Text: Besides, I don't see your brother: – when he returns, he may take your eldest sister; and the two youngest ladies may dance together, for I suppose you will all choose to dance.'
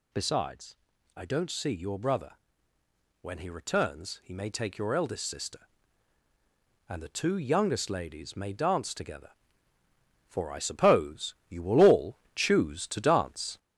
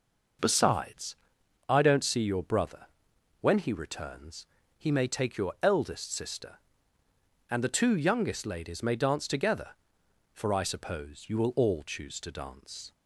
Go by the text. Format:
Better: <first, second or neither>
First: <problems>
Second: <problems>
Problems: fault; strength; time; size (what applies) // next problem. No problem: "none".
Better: second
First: gets louder; throughout; 3.5 dB // pauses between "all" and "choose"; slight; at 12.1 s; 0.18 s long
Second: none